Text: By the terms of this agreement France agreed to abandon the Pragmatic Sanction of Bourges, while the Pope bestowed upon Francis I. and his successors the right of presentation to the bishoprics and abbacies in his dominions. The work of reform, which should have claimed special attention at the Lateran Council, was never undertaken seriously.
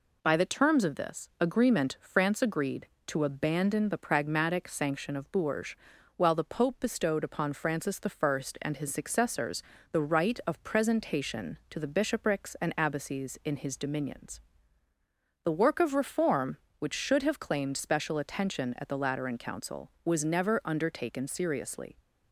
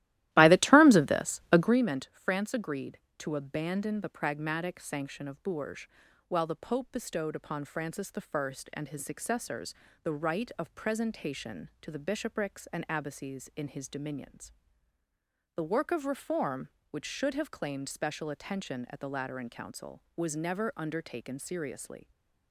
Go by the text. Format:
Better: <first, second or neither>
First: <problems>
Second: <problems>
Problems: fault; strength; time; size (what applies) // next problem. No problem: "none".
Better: first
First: pauses between "successors" and "the"; slight; at 9.6 s; 0.30 s long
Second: starts louder than the rest; strong; until 1.8 s; 15 dB // pauses between "successors" and "the"; slight; at 9.7 s; 0.30 s long